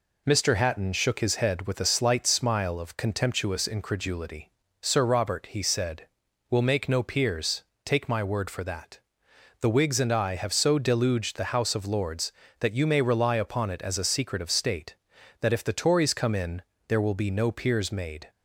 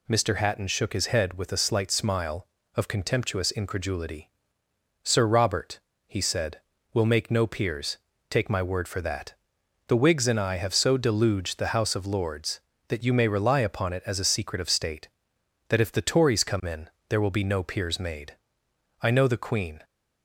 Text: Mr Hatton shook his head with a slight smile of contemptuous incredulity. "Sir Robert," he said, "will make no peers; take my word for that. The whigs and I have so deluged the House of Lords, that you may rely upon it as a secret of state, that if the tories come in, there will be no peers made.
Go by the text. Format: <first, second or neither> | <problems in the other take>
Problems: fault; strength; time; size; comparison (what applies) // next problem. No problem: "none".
first | goes on to say "I know the Queen"; noticeable; from 19.0 s on; 0.82 s long